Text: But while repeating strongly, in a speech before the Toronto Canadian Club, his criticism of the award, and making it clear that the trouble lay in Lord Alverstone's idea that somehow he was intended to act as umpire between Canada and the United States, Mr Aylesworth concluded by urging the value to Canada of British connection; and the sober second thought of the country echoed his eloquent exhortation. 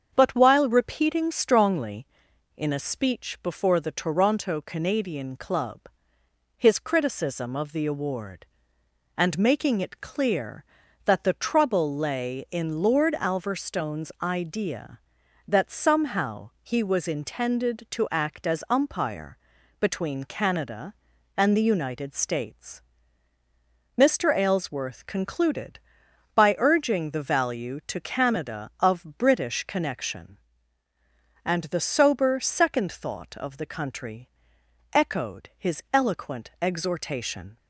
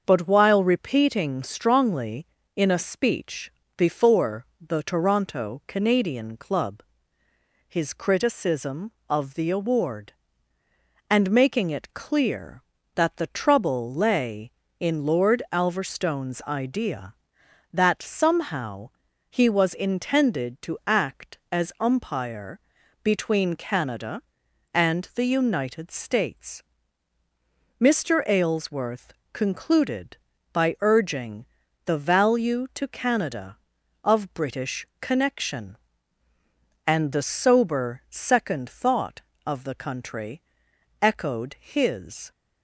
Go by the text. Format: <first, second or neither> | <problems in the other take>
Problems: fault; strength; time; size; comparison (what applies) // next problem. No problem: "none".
first | starts louder than the rest; until 1.0 s; 6.5 dB; also in the first // pauses between "speech" and "before"; slight; at 3.5 s; 0.26 s long // pauses between "before" and "the"; slight; at 4.4 s; 0.20 s long // pauses between "somehow" and "he"; at 18.9 s; 0.38 s long // pauses between "umpire" and "between"; at 22.5 s; 0.44 s long; also in the first // pauses between "Aylesworth" and "concluded"; slight; at 29.1 s; 0.20 s long // pauses between "urging" and "the"; at 31.4 s; 0.42 s long // pauses between "country" and "echoed"; noticeable; at 40.4 s; 0.62 s long; noticeable in the first // stops before "eloquent exhortation"; at 42.3 s